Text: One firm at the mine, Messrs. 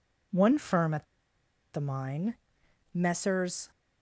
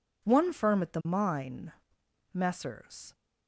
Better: second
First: pauses between "at" and "the"; noticeable; at 1.0 s; 0.67 s long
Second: none

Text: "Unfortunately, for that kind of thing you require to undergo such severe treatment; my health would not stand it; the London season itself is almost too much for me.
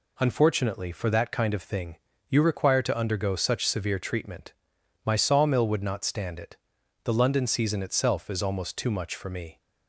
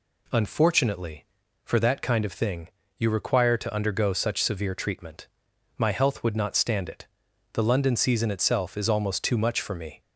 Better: second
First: pauses between "thing" and "you"; slight; at 1.9 s; 0.30 s long // says "sawmill" for "health"; at 5.1 s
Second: pauses between "thing" and "you"; slight; at 2.6 s; 0.30 s long

